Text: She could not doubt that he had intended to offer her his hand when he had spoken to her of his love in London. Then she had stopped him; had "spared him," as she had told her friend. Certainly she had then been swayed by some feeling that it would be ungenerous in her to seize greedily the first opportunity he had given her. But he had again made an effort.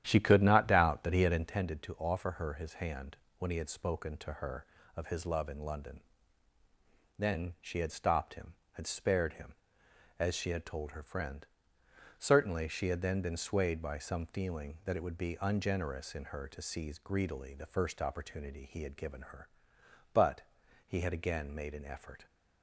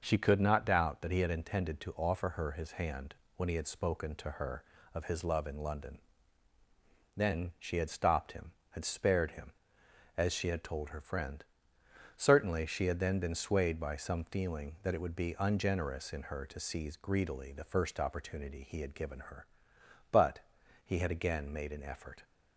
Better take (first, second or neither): second